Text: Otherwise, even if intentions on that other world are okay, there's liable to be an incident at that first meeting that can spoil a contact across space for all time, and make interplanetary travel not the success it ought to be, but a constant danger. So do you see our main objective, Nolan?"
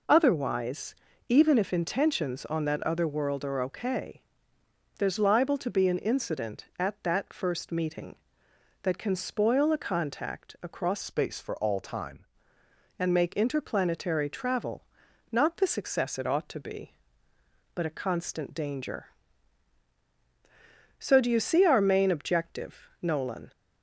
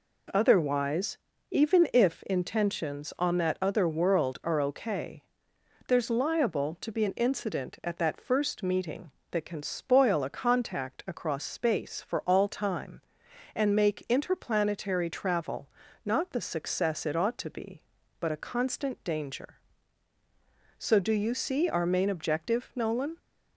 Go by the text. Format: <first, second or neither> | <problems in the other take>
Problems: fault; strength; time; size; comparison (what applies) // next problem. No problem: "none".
second | changes voice from "space" to "time"; from 11.0 to 12.2 s; 1.2 s long // pauses between "travel" and "not"; noticeable; at 14.8 s; 0.48 s long; slight in the second